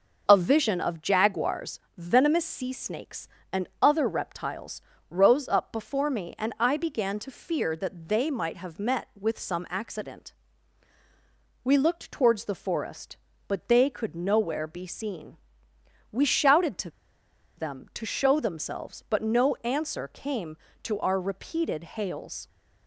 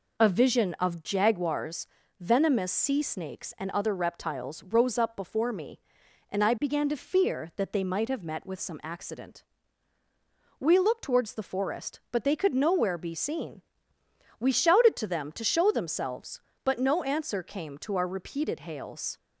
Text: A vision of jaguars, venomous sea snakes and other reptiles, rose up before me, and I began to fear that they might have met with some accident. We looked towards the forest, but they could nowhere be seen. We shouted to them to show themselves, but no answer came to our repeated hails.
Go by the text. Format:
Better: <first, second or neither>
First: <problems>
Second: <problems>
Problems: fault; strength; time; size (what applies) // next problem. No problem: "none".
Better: second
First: pauses between "to" and "them"; noticeable; at 16.9 s; 0.66 s long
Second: none